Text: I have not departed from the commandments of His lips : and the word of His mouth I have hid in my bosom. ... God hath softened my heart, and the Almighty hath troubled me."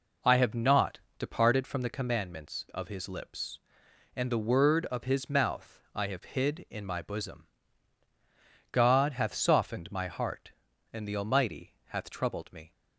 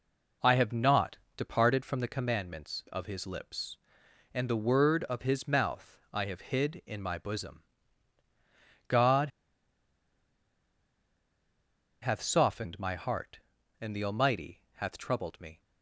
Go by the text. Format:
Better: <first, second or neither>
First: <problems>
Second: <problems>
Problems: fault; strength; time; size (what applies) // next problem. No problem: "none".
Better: first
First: pauses between "not" and "departed"; slight; at 0.9 s; 0.18 s long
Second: pauses between "not" and "departed"; slight; at 1.1 s; 0.18 s long // pauses between "God" and "hath"; strong; at 9.2 s; 2.7 s long